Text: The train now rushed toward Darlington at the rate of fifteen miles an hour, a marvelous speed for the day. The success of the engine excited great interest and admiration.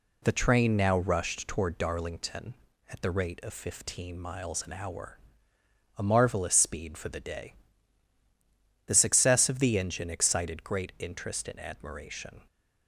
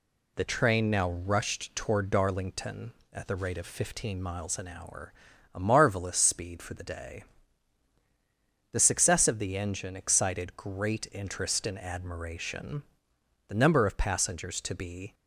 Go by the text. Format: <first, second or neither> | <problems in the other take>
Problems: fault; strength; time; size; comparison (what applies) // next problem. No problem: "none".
first | goes on to say "The number of passengers to be"; from 13.4 s on; 1.6 s long